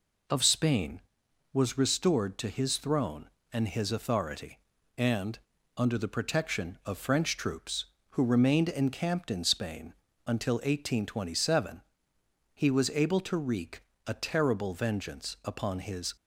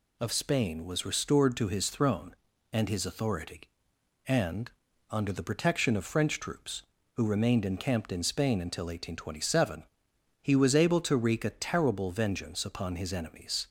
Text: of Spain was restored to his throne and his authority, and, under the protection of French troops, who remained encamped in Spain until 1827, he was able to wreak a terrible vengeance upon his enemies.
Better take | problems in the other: second | pauses between "Spain" and "until"; slight; at 9.9 s; 0.34 s long // pauses between "wreak" and "a"; slight; at 13.8 s; 0.24 s long // stops before "enemies"; at 16.1 s

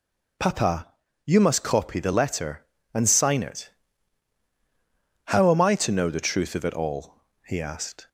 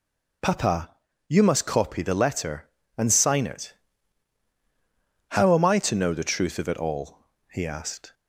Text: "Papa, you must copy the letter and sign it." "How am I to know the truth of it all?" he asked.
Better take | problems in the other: neither | none

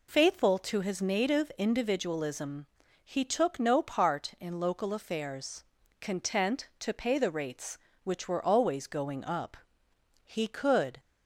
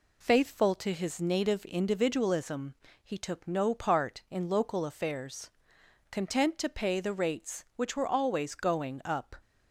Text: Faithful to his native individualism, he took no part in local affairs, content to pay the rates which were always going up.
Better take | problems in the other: second | goes on to say "He could"; noticeable; from 10.2 s on; 0.74 s long

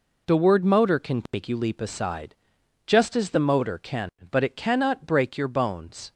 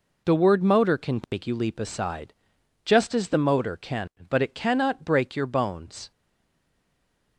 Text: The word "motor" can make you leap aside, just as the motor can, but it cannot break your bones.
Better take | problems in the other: first | stays silent after the last word; noticeable; from 6.1 s on; 1.2 s long

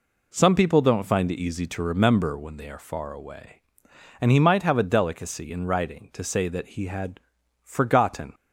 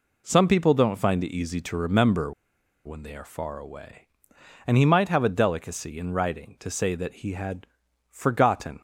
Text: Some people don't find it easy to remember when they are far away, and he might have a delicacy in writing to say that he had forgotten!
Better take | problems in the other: first | pauses between "remember" and "when"; noticeable; at 2.3 s; 0.52 s long // pauses between "had" and "forgotten"; noticeable; at 7.6 s; 0.46 s long; noticeable in the first

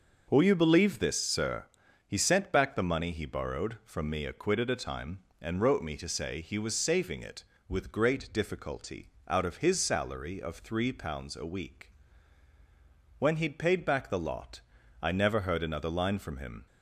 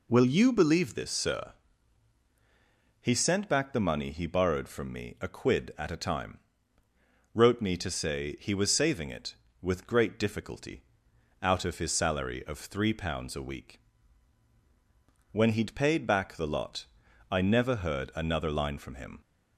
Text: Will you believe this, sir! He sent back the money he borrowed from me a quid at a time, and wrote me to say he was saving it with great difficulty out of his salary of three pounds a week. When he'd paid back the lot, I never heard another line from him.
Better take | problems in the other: first | skips "and"; at 6.8 s // pauses between "difficulty" and "out"; noticeable; at 10.8 s; 0.62 s long; slight in the first

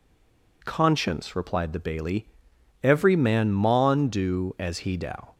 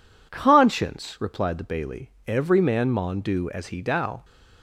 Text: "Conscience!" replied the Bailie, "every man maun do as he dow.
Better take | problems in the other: second | stays silent before the first word; slight; until 0.6 s; 0.6 s long

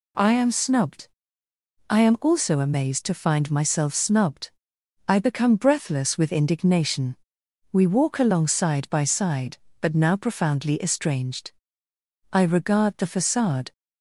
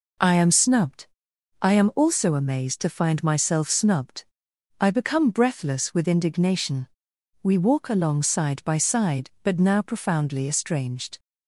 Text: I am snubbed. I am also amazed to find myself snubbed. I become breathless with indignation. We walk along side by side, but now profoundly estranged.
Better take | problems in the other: second | goes on to say "I regard the facade"; from 12.3 s on; 1.4 s long

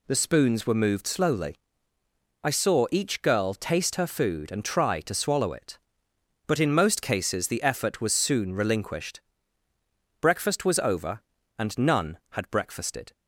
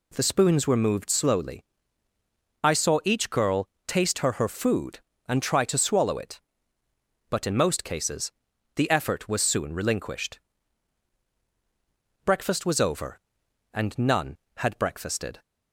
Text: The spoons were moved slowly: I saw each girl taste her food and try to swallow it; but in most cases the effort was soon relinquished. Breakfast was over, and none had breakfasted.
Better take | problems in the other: first | pauses between "girl" and "taste"; slight; at 3.6 s; 0.20 s long // says "her" twice; at 4.3 s // pauses between "cases" and "the"; at 8.3 s; 0.44 s long

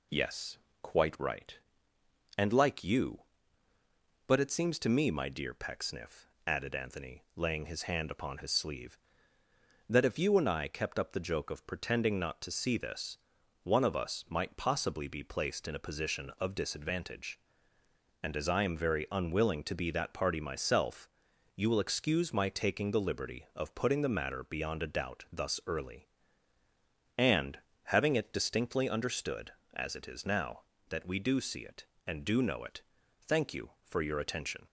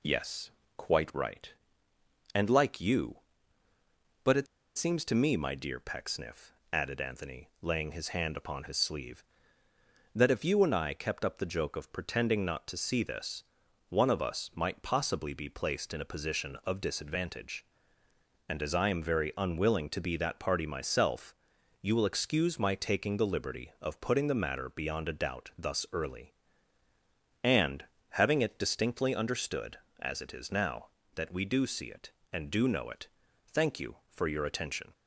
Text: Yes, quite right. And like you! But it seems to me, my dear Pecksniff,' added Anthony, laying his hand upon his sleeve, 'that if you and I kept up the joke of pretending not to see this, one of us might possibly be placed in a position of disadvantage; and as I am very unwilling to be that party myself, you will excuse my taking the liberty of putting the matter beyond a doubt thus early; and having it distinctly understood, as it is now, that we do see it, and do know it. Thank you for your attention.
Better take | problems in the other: first | pauses between "it" and "seems"; slight; at 4.4 s; 0.31 s long // pauses between "and" and "having"; slight; at 27.8 s; 0.26 s long; slight in the first

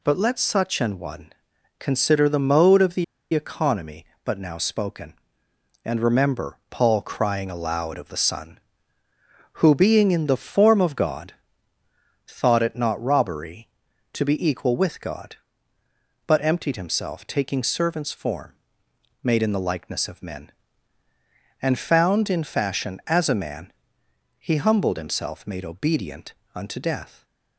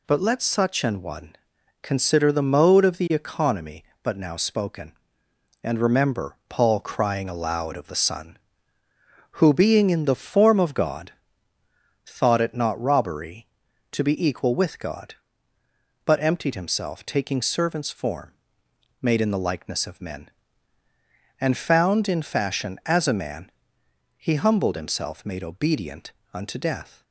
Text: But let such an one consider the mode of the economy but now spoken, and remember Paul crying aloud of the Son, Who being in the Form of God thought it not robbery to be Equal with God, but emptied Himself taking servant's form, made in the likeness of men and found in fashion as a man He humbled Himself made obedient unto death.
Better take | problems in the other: second | pauses between "one" and "consider"; noticeable; at 1.3 s; 0.46 s long; noticeable in the second // pauses between "the" and "economy"; slight; at 3.0 s; 0.29 s long // pauses between "God" and "thought"; noticeable; at 11.3 s; 0.94 s long; noticeable in the second // pauses between "man" and "He"; noticeable; at 23.7 s; 0.66 s long; noticeable in the second // pauses between "obedient" and "unto"; slight; at 26.3 s; 0.20 s long; slight in the second

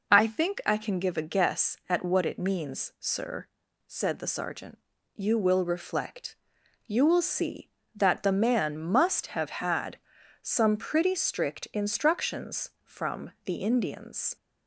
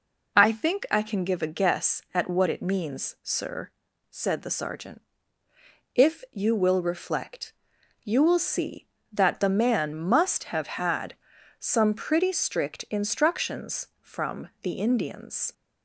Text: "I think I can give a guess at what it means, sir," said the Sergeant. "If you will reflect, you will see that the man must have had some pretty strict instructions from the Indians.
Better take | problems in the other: second | skips "If"; at 4.9 s // pauses between "had" and "some"; at 9.9 s; 0.44 s long; also in the second

